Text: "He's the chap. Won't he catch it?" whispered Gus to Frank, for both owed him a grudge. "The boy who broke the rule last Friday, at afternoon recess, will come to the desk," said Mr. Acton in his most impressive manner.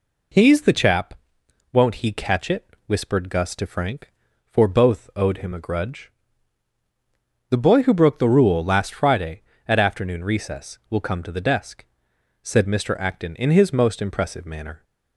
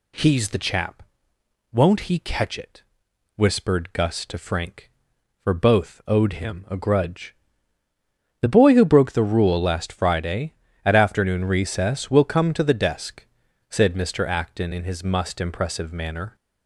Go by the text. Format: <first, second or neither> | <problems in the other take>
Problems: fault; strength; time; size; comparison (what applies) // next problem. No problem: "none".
first | says "must" for "most"; at 15.0 s